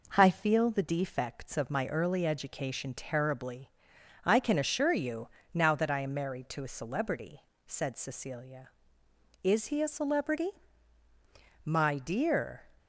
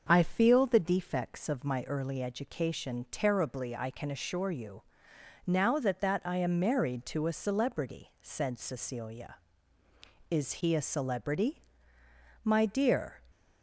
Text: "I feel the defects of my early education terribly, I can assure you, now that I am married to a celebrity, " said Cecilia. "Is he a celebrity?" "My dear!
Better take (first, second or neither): first